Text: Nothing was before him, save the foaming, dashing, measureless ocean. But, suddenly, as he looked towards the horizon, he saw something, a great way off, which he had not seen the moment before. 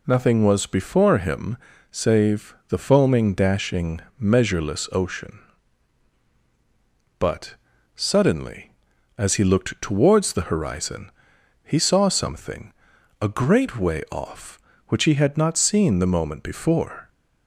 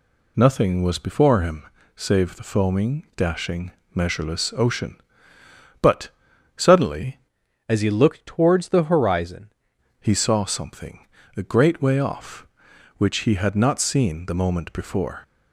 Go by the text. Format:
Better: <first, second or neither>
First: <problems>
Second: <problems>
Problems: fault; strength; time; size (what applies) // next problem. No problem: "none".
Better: first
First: none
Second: changes voice from "as" to "horizon"; from 7.6 to 9.5 s; 1.9 s long